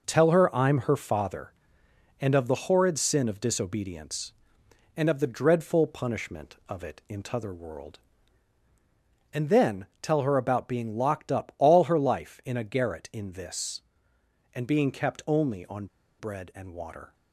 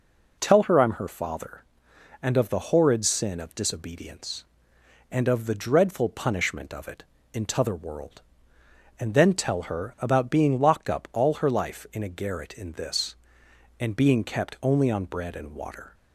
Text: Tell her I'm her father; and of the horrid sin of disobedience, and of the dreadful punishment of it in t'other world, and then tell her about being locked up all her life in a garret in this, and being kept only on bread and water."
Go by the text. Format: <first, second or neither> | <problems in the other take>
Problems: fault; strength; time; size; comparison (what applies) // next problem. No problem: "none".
second | pauses between "then" and "tell"; slight; at 9.8 s; 0.16 s long // pauses between "on" and "bread"; slight; at 15.8 s; 0.33 s long